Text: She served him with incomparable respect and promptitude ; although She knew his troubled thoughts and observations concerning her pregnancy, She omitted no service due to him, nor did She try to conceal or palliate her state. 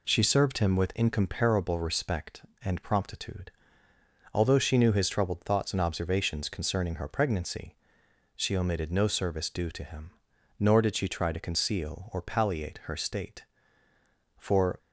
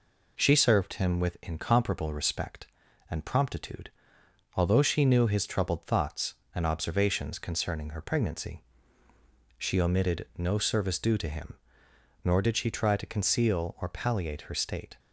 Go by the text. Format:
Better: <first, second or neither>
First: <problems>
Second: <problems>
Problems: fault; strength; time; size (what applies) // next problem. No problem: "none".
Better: second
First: goes on to say "For"; slight; from 14.3 s on; 0.40 s long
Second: none